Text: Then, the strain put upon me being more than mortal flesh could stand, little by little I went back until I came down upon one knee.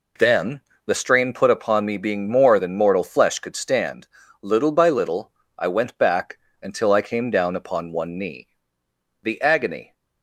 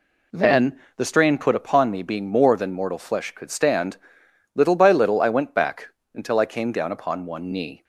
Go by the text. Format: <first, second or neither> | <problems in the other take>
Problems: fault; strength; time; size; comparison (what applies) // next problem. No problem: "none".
second | pauses between "little" and "I"; slight; at 5.3 s; 0.26 s long // pauses between "back" and "until"; slight; at 6.3 s; 0.24 s long; slight in the second // goes on to say "The agony"; noticeable; from 9.2 s on; 0.70 s long